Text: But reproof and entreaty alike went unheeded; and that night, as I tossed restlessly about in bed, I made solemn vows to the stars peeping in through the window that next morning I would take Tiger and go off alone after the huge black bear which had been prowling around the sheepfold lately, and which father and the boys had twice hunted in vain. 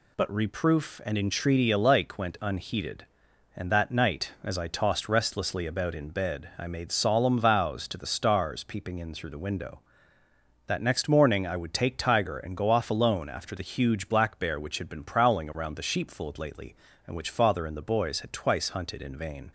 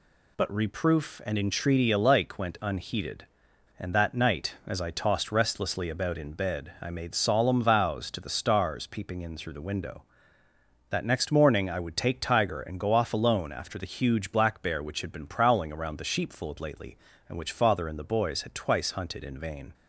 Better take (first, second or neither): neither